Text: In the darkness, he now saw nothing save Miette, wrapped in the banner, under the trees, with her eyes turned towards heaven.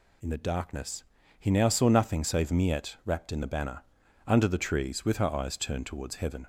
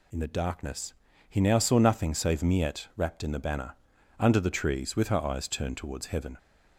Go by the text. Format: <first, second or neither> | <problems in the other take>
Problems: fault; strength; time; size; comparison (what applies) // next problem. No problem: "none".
neither | none